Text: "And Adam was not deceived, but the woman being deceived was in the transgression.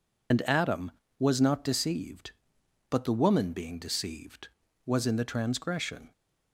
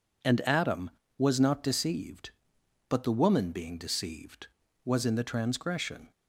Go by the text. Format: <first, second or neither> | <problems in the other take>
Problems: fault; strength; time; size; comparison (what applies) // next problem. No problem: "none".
second | loses the start of "And"; at 0.3 s; 65 ms